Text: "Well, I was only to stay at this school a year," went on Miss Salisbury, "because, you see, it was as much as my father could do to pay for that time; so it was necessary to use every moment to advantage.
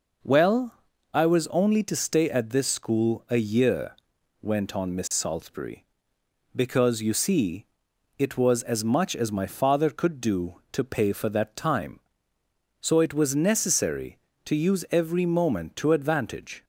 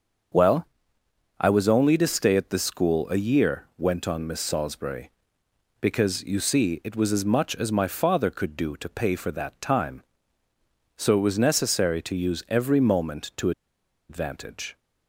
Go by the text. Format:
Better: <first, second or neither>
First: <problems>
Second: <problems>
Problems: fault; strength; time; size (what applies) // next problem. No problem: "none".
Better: first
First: none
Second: starts louder than the rest; until 2.0 s; 6.5 dB // pauses between "to" and "advantage"; noticeable; at 13.5 s; 0.58 s long